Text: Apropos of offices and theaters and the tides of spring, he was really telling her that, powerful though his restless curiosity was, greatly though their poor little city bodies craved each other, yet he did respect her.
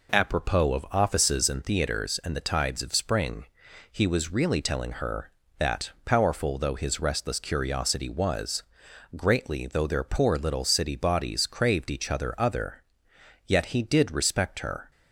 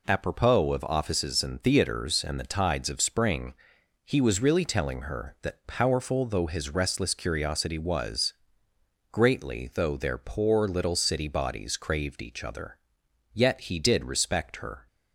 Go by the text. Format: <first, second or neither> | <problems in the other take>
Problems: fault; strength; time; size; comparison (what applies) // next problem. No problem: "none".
second | says "other" twice; at 12.3 s